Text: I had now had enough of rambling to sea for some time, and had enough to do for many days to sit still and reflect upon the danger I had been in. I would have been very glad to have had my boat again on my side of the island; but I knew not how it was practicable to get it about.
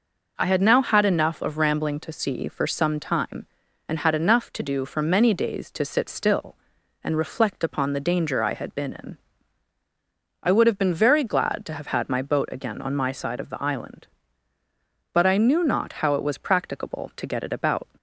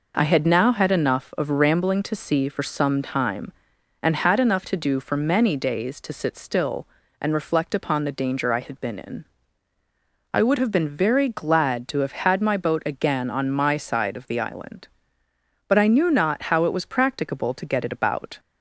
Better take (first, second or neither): neither